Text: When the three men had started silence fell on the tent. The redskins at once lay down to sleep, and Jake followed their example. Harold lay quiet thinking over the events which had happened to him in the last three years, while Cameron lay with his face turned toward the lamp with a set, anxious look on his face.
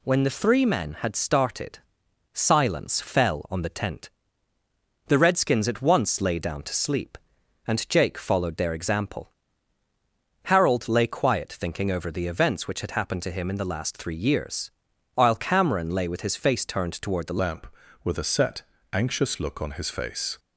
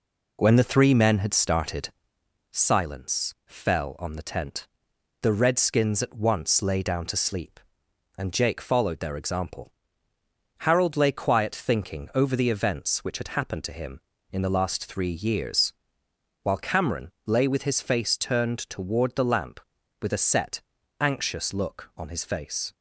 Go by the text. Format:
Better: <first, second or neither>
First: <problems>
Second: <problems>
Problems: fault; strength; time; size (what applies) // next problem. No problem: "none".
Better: second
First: pauses between "started" and "silence"; noticeable; at 1.8 s; 0.52 s long // changes voice at "lamp"; from 17.4 s on; 2.9 s long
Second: pauses between "started" and "silence"; noticeable; at 1.8 s; 0.60 s long